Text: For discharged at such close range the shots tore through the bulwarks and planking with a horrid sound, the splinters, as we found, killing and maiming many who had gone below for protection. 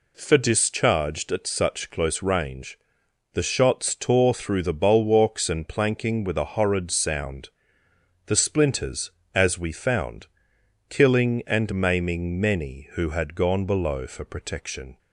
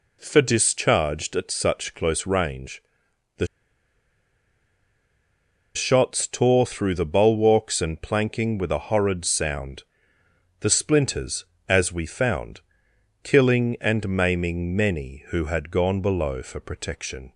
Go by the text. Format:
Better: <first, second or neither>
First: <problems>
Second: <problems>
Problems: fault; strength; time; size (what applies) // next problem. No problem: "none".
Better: first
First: pauses between "range" and "the"; noticeable; at 2.7 s; 0.56 s long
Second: pauses between "range" and "the"; noticeable; at 2.8 s; 0.56 s long // pauses between "the" and "shots"; strong; at 3.4 s; 2.2 s long